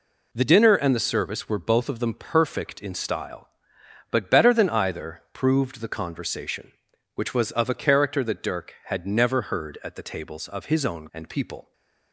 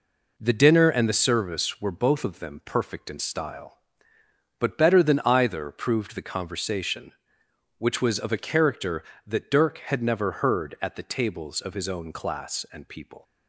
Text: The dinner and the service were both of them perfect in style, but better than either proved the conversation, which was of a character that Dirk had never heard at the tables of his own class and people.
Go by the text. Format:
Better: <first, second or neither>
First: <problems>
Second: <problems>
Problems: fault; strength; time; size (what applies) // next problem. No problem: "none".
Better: second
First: skips "class"; at 11.0 s // stays silent after the last word; slight; from 11.6 s on; 0.5 s long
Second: none